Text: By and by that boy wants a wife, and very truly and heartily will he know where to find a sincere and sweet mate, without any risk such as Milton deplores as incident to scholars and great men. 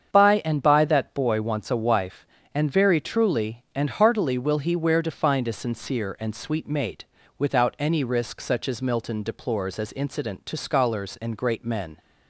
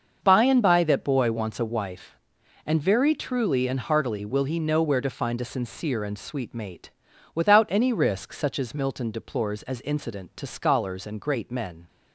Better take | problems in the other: second | starts louder than the rest; strong; until 1.1 s; 7.5 dB; also in the second // skips "know"; at 4.7 s

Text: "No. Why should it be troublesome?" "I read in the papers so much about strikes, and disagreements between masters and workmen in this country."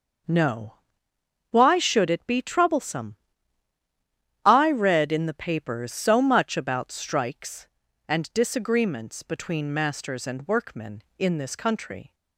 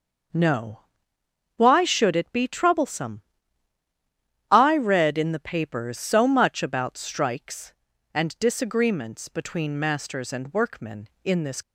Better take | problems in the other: first | starts louder than the rest; until 2.0 s; 6.5 dB; also in the first // stops before "country"; at 11.6 s

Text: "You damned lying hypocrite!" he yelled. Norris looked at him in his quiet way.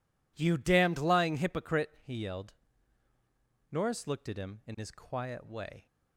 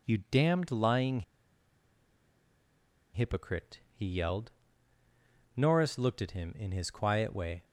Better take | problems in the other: first | pauses between "lying" and "hypocrite"; strong; at 1.2 s; 1.9 s long

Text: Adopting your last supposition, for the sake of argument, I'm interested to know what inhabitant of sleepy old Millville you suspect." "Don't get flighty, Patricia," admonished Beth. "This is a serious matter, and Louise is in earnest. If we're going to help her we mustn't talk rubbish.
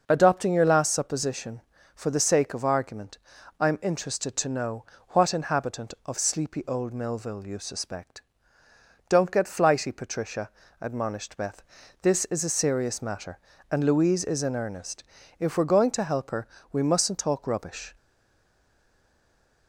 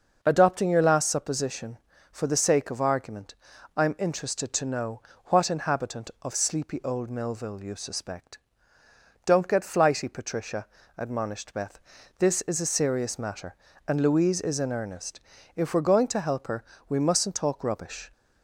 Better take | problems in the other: second | pauses between "know" and "what"; slight; at 4.8 s; 0.24 s long; slight in the second // pauses between "her" and "we"; slight; at 16.4 s; 0.24 s long; slight in the second // stays silent after the last word; noticeable; from 17.9 s on; 1.7 s long

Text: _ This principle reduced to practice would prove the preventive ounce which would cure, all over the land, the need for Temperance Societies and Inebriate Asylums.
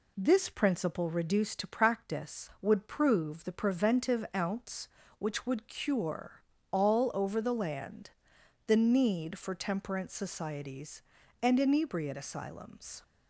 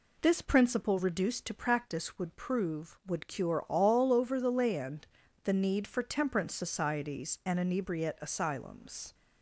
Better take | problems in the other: first | skips "the preventive ounce which"; at 3.0 s

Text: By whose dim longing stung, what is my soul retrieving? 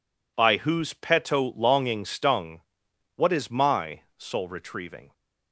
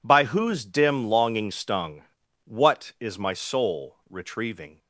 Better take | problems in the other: second | says "peto" for "dim"; at 0.9 s // pauses between "my" and "soul"; slight; at 4.0 s; 0.16 s long

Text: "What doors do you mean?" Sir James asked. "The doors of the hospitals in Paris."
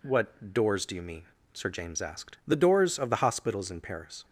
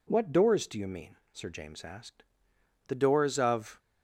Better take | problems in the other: first | stops before "the hospitals in Paris"; at 3.7 s

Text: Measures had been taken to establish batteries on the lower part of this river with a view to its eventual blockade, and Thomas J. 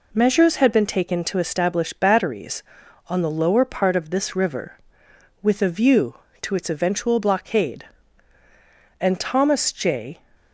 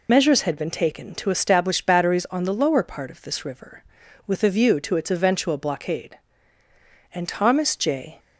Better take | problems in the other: first | loses the start of "Measures"; at 0.0 s; 60 ms

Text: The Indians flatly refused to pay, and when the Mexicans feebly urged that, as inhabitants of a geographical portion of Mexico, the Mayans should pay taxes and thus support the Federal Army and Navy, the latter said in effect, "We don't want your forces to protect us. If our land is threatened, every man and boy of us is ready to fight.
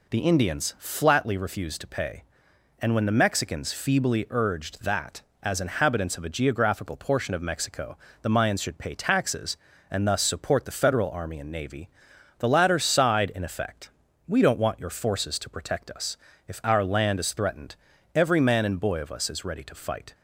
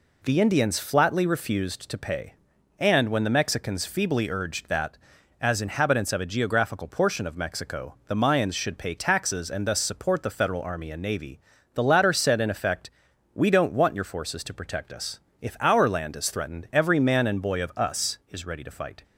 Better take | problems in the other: second | says "sighed" for "said"; at 12.7 s

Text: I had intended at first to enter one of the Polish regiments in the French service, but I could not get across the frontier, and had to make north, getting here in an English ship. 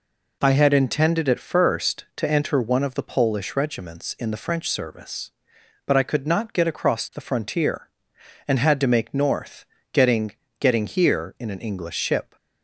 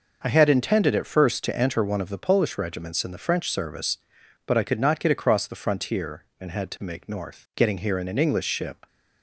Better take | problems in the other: second | says "getting" twice; at 10.5 s

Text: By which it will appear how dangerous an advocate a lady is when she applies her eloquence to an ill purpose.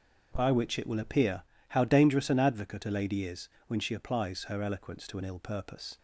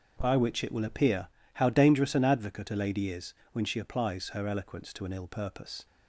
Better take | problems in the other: neither | starts louder than the rest; noticeable; the same in both // pauses between "appear" and "how"; slight; the same in both // pauses between "is" and "when"; slight; the same in both

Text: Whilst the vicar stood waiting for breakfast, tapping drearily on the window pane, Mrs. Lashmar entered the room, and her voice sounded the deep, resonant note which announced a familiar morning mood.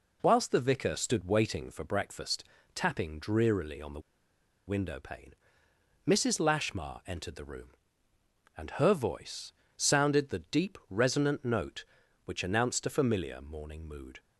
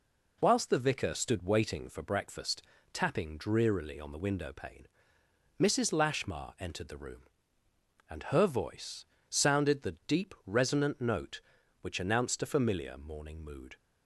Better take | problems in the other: second | pauses between "the" and "window"; noticeable; at 3.9 s; 0.67 s long // pauses between "voice" and "sounded"; slight; at 9.5 s; 0.24 s long; slight in the second

